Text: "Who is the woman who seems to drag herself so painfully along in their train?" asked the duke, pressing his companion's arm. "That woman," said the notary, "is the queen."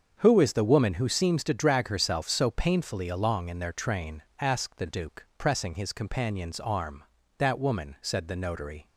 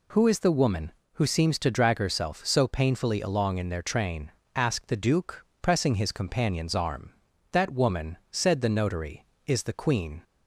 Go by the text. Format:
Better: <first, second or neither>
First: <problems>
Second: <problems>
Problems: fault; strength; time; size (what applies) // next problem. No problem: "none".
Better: second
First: starts louder than the rest; until 1.2 s; 7 dB // stops before "is the queen"; at 8.8 s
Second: none